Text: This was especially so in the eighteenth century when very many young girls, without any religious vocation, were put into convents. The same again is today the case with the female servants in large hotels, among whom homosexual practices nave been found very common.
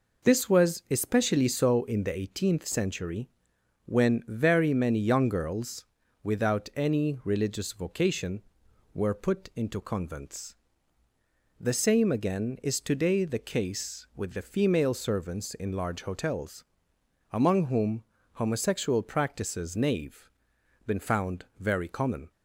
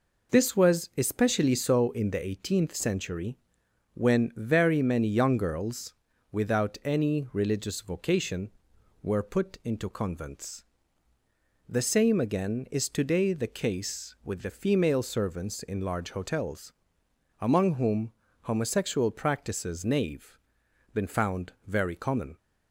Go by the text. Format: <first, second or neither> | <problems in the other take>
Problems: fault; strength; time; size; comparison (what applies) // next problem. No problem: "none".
neither | pauses between "century" and "when"; noticeable; the same in both // pauses between "whom" and "homosexual"; slight; the same in both // pauses between "nave" and "been"; noticeable; the same in both